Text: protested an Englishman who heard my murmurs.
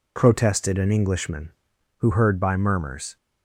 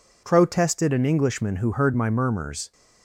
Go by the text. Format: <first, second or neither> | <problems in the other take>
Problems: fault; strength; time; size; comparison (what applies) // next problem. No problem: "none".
second | says "by" for "my"; at 2.4 s